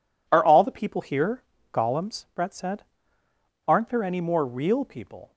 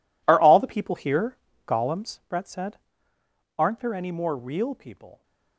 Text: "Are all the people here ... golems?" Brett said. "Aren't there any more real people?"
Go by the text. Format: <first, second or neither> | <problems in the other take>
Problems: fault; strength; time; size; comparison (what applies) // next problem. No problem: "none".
first | gets quieter; strong; throughout; 14.5 dB